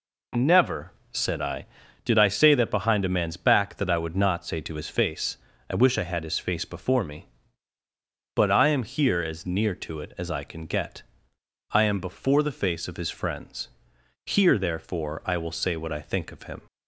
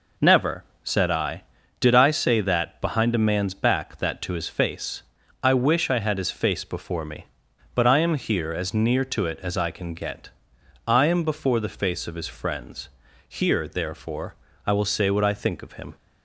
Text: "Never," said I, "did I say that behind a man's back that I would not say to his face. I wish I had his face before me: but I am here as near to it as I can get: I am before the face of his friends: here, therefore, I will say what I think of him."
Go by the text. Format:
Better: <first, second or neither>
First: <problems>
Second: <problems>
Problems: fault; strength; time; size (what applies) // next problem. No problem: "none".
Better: first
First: none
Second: skips "I would not say"; at 4.2 s